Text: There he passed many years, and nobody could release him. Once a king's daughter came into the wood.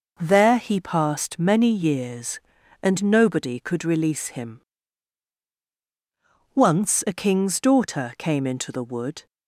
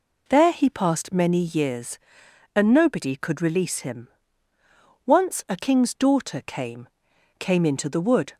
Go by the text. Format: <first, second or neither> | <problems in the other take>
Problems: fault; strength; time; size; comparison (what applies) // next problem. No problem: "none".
first | says "came" twice; at 7.3 s